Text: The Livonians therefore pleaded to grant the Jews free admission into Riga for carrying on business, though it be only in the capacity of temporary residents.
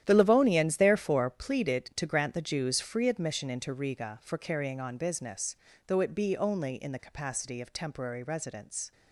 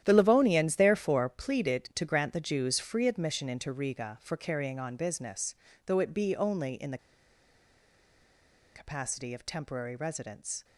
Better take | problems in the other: first | starts louder than the rest; strong; until 1.0 s; 11 dB; strong in the first // pauses between "the" and "capacity"; strong; at 6.9 s; 1.7 s long

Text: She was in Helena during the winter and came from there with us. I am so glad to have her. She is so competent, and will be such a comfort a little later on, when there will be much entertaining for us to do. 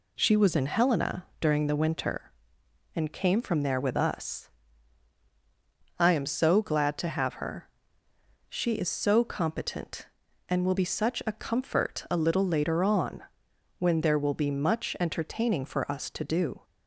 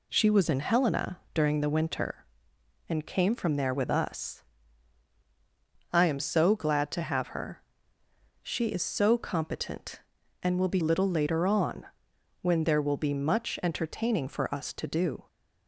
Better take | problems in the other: first | pauses between "Helena" and "during"; slight; at 1.1 s; 0.16 s long; slight in the first // skips "such a comfort a"; at 10.7 s

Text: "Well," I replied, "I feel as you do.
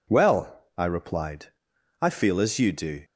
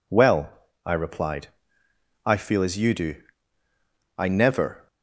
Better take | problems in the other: first | goes on to say "I never"; noticeable; from 4.1 s on; 0.70 s long

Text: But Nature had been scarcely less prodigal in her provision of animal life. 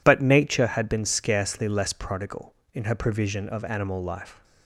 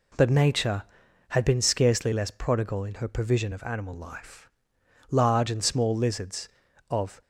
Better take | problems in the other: first | goes on to say "Large and small lizards of"; strong; from 5.0 s on; 2.1 s long

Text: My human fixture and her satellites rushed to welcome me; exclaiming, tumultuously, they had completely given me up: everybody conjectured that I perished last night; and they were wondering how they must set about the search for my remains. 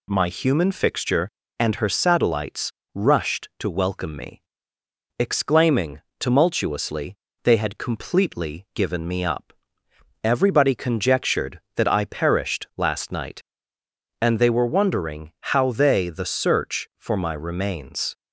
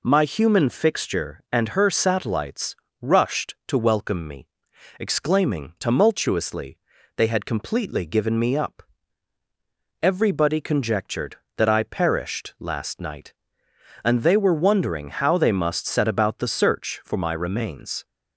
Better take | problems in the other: second | pauses between "satellites" and "rushed"; slight; at 2.7 s; 0.24 s long; slight in the second // pauses between "wondering" and "how"; slight; at 15.3 s; 0.22 s long // skips "must set about"; at 16.0 s

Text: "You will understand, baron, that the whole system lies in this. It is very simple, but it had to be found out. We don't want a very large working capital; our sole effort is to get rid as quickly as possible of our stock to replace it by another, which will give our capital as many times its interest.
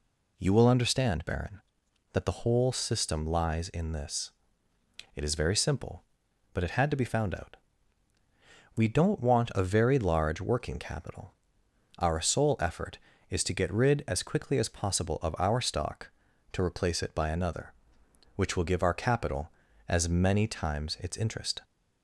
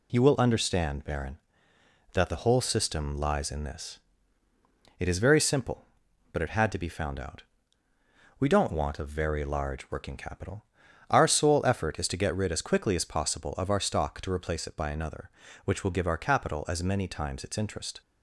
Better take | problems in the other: neither | none

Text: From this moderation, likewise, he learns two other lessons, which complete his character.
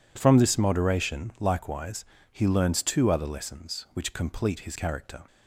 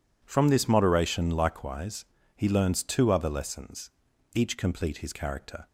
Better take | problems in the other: first | says "each" for "which"; at 4.3 s

